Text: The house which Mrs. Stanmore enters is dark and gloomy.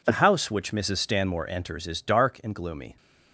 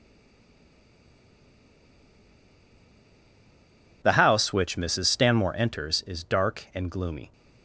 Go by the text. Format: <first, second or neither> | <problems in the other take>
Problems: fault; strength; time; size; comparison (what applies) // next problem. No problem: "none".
first | stays silent before the first word; strong; until 4.0 s; 4.0 s long